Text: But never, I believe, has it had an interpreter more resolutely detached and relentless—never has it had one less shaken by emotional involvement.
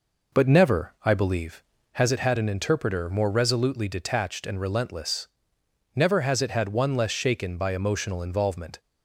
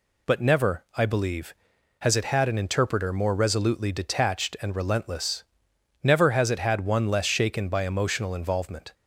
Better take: second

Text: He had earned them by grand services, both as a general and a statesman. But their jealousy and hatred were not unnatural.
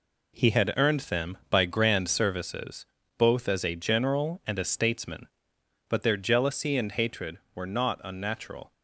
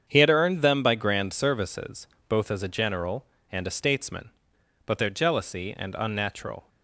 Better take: first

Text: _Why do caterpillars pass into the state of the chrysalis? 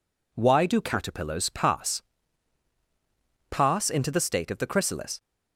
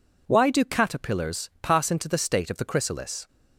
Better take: second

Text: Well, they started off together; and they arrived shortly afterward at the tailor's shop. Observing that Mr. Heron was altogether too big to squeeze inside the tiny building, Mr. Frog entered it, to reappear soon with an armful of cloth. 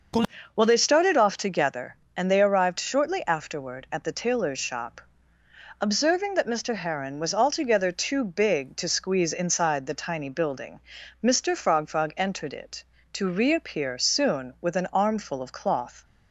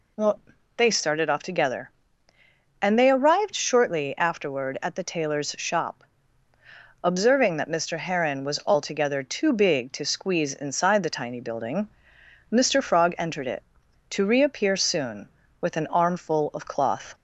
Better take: second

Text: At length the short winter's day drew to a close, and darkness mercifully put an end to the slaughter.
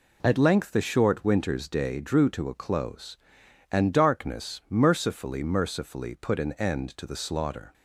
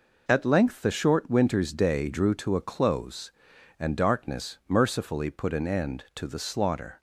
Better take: second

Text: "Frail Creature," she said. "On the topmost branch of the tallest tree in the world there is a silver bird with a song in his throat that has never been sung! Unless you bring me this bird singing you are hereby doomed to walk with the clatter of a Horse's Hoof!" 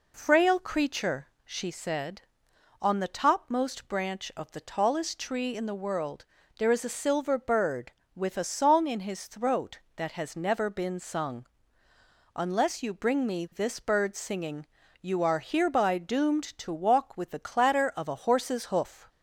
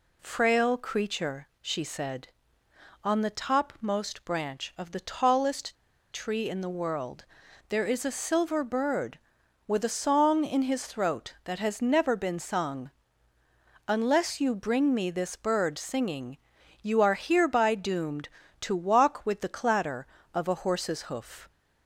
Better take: first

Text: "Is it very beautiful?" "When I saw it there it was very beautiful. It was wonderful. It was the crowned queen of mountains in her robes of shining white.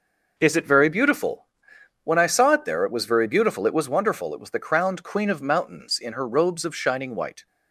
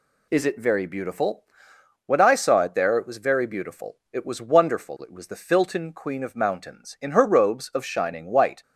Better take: first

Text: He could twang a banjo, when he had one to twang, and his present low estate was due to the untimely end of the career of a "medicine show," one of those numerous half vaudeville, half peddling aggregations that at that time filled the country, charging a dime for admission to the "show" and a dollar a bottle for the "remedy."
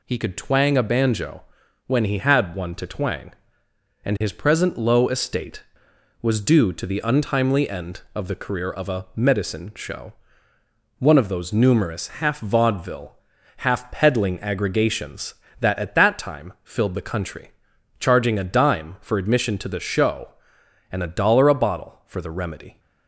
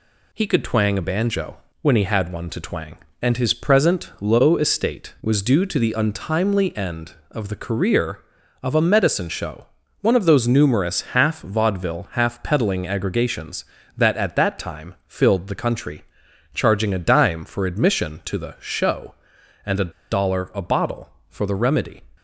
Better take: first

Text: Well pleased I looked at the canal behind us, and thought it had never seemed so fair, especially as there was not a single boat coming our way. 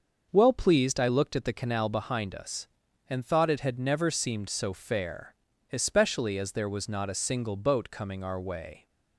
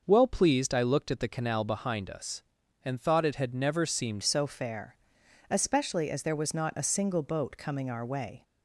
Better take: first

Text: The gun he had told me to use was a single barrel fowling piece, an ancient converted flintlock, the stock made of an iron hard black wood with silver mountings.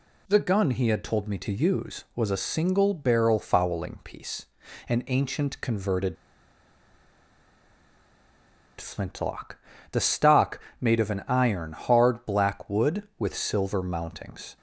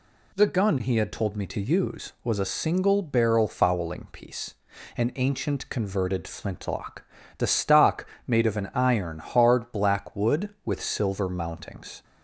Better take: second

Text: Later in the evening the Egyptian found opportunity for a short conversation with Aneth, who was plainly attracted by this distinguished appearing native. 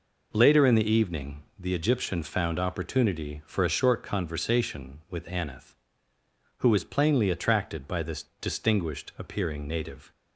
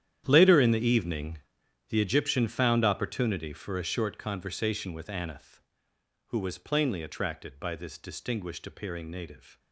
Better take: first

